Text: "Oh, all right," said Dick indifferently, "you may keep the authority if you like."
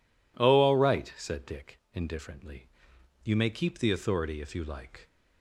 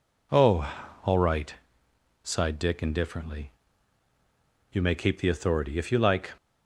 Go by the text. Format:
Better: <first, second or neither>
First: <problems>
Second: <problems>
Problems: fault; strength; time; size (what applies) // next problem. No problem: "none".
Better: first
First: none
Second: says "sighed" for "said"; at 2.2 s